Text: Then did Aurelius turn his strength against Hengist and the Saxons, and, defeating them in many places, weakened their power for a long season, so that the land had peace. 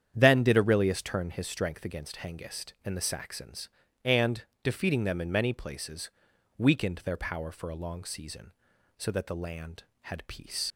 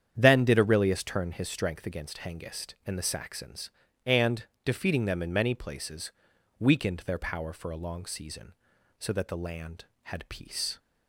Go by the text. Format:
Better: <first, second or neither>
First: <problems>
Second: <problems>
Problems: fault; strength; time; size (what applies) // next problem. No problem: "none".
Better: second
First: starts louder than the rest; strong; until 1.1 s; 8.5 dB // leaves "peace" unfinished; at 10.7 s; 65 ms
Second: starts louder than the rest; strong; until 1.1 s; 8.5 dB